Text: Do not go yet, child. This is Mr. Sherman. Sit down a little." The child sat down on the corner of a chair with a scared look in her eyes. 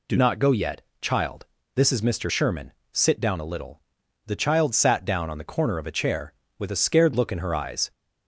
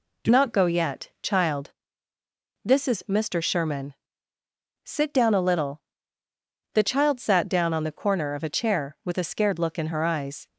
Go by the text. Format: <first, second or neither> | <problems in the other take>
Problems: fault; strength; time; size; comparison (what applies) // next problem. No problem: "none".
first | changes voice at "not"; from 0.2 s on; 10.2 s long